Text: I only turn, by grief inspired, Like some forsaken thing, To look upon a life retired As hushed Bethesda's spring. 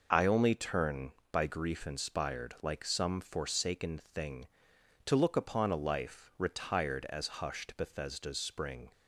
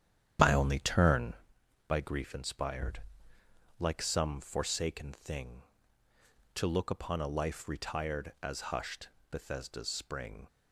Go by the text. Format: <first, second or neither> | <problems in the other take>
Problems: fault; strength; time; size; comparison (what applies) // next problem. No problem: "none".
first | starts louder than the rest; strong; until 1.6 s; 8.5 dB // pauses between "hushed" and "Bethesda's"; slight; at 9.0 s; 0.22 s long